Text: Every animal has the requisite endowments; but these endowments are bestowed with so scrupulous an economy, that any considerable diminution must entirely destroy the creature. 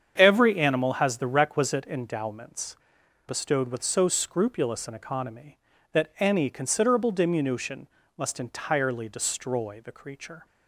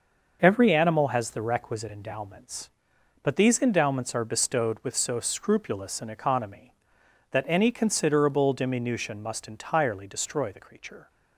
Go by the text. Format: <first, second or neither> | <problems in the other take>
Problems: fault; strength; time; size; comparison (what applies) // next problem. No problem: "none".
second | starts louder than the rest; strong; until 1.1 s; 7.5 dB; noticeable in the second // skips "but these endowments are"; at 3.0 s // pauses between "diminution" and "must"; slight; at 7.8 s; 0.30 s long